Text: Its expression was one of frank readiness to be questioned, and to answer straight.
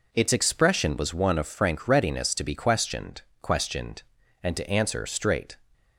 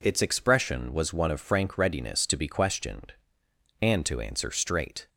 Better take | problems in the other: second | says "questioned" twice; at 3.4 s

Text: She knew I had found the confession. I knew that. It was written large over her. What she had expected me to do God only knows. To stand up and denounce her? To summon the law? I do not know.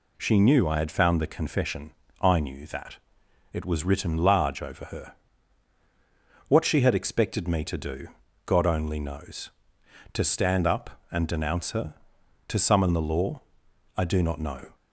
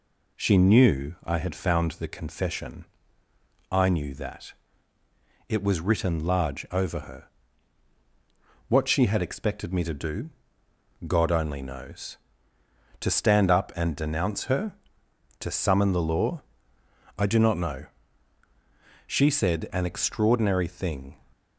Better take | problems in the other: first | pauses between "do" and "God"; noticeable; at 10.2 s; 0.76 s long; also in the first // goes on to say "She said an extraordinary thing"; strong; from 19.0 s on; 2.1 s long

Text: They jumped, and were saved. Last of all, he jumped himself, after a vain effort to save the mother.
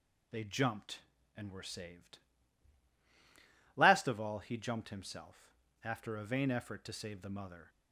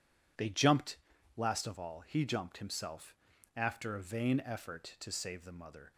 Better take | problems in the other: first | skips "and were saved"; at 1.1 s

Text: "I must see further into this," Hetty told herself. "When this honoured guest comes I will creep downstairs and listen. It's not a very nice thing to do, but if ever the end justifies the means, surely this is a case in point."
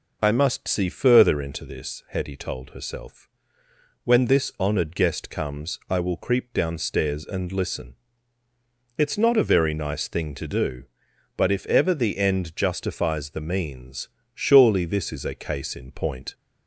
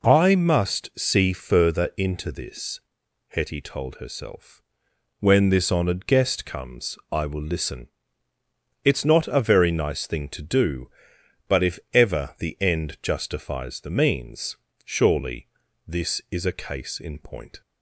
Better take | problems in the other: first | skips "creep downstairs and"; at 7.4 s // pauses between "if" and "ever"; slight; at 11.7 s; 0.16 s long // pauses between "surely" and "this"; at 15.4 s; 0.40 s long

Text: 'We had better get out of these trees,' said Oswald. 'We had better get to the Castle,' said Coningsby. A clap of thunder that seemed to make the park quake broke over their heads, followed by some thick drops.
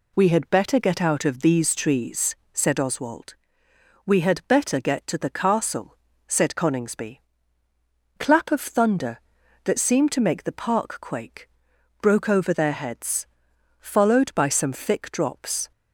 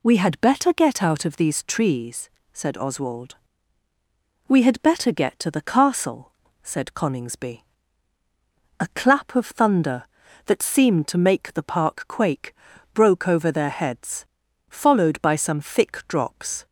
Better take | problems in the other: second | skips "A"; at 7.6 s // pauses between "quake" and "broke"; noticeable; at 11.4 s; 0.54 s long; also in the second

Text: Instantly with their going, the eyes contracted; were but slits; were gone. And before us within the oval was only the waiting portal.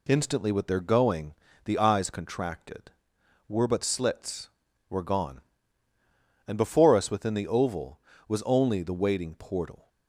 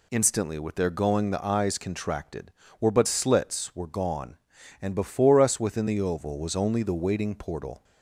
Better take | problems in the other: neither | none

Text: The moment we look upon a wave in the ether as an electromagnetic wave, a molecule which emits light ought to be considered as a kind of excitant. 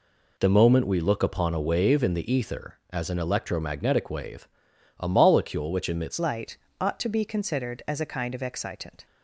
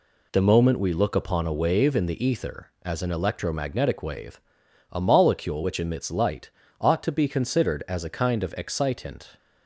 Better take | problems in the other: second | changes voice at "light"; from 6.1 s on; 2.9 s long // pauses between "light" and "ought"; slight; at 6.5 s; 0.24 s long; slight in the second

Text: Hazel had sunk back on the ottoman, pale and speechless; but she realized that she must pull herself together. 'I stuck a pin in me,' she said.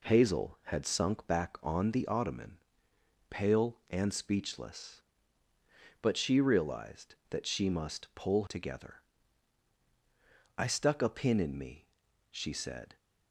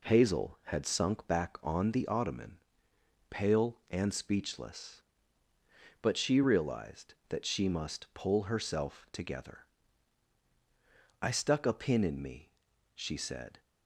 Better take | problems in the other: second | skips "herself"; at 8.4 s

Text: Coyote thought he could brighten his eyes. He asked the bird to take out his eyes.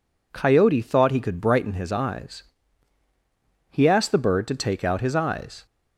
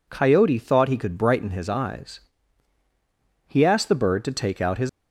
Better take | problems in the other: first | stops before "eyes"; at 4.8 s

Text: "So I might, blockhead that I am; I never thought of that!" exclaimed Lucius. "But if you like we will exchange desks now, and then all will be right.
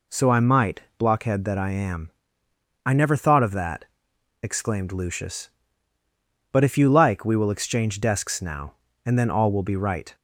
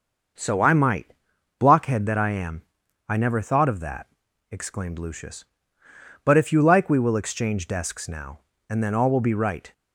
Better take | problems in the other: neither | none

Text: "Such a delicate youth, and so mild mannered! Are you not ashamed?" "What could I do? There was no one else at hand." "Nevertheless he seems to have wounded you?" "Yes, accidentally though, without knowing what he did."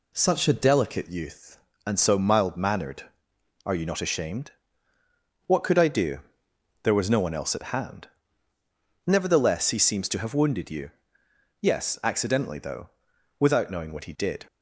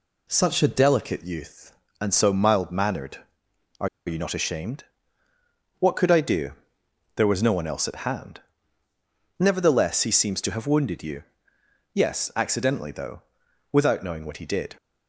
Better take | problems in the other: first | pauses between "Are" and "you"; slight; at 3.8 s; 0.19 s long

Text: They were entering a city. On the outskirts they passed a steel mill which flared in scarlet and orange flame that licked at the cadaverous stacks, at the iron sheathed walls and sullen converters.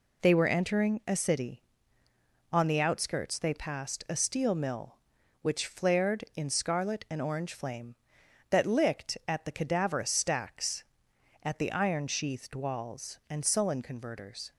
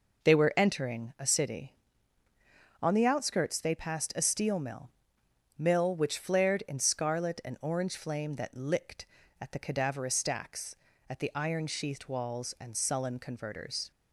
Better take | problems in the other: first | says "mill" twice; at 5.5 s

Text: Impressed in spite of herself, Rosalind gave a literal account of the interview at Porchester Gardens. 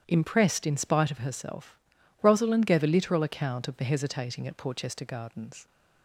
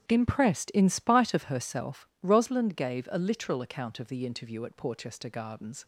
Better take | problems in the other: second | starts louder than the rest; strong; until 1.0 s; 9.5 dB; strong in the second // says "hesitating" for "interview"; at 3.8 s

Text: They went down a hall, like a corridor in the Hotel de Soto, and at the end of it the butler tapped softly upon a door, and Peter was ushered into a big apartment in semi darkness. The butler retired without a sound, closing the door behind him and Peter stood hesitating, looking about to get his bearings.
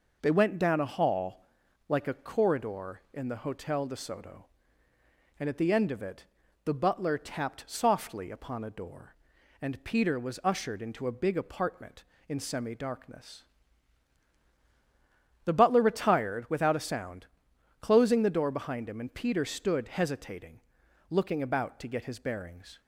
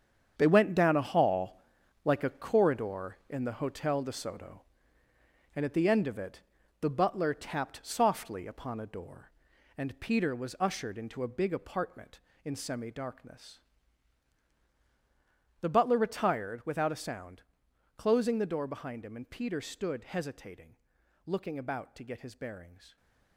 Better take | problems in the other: first | gets quieter; strong; throughout; 10 dB // pauses between "it" and "the"; at 6.4 s; 0.38 s long; also in the first

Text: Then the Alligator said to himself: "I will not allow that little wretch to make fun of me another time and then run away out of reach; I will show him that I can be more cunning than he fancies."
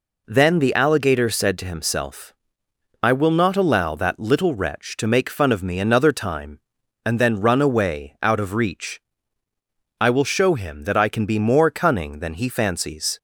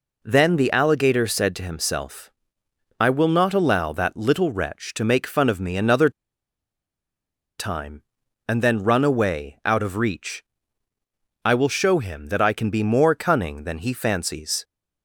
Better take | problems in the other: first | pauses between "another" and "time"; strong; at 6.0 s; 1.4 s long

